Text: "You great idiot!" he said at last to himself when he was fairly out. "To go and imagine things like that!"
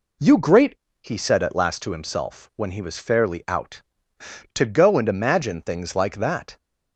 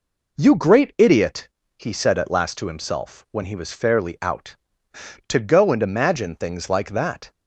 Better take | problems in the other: second | skips "idiot"; at 0.8 s

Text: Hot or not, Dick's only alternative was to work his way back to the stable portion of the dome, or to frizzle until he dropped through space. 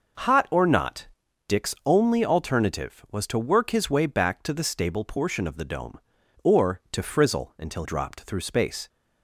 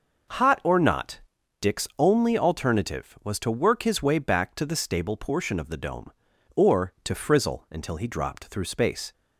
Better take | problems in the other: second | skips "he"; at 7.8 s

